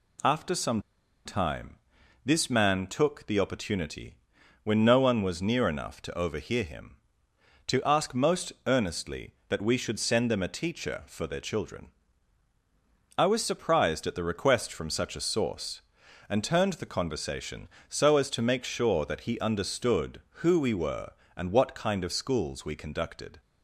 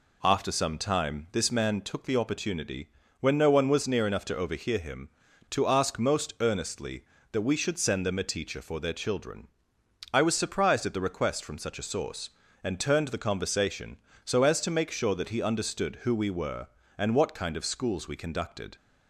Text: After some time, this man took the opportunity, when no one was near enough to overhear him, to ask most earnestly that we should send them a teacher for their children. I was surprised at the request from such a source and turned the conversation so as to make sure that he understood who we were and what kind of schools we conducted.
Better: second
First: pauses between "some" and "time"; at 0.8 s; 0.43 s long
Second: none

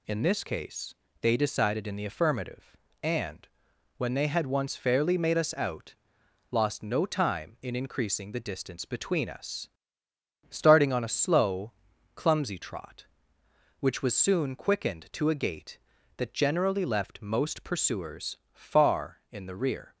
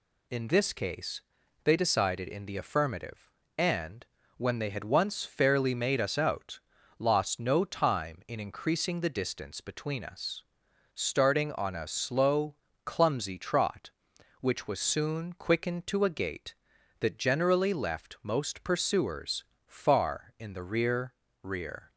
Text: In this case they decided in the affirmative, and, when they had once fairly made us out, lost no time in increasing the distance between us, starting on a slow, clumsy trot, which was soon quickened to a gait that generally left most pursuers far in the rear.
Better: first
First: pauses between "case" and "they"; slight; at 0.9 s; 0.26 s long // pauses between "pursuers" and "far"; slight; at 18.3 s; 0.16 s long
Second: pauses between "case" and "they"; at 1.2 s; 0.42 s long // pauses between "pursuers" and "far"; slight; at 19.4 s; 0.22 s long // says "rear" twice; at 21.4 s

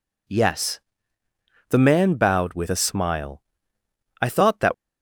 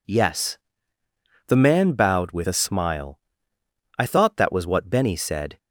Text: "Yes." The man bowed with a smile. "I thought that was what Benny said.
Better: second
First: stops before "was what Benny said"; at 4.7 s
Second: none

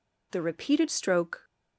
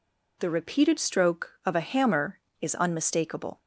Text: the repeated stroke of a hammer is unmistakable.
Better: second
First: stops before "of a hammer is unmistakable"; at 1.4 s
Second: none

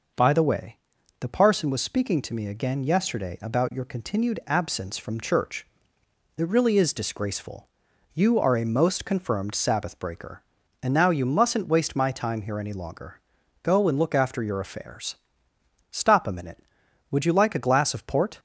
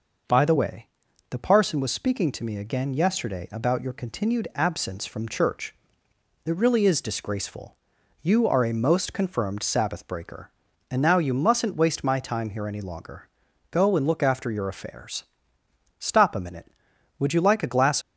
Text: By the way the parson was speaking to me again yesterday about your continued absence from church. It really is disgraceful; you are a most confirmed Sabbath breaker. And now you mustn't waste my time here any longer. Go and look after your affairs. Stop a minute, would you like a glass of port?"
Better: first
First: pauses between "way" and "the"; at 0.7 s; 0.42 s long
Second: pauses between "way" and "the"; at 0.8 s; 0.42 s long // stops before "of port"; at 18.0 s

